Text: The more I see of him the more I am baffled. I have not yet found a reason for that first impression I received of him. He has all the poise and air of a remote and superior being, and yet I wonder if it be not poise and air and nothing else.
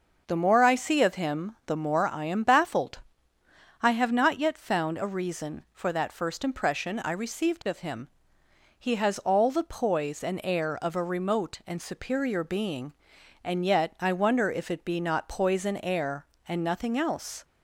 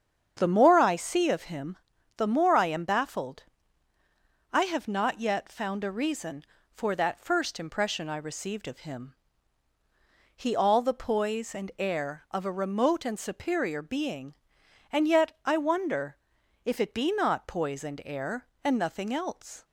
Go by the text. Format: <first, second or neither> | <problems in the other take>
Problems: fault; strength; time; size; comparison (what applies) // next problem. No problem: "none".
first | starts louder than the rest; strong; until 1.3 s; 7.5 dB // pauses between "him" and "the"; at 1.7 s; 0.38 s long // skips "has"; at 10.5 s // pauses between "wonder" and "if"; noticeable; at 16.1 s; 0.48 s long